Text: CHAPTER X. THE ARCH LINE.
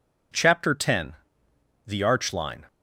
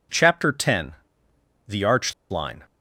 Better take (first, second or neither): first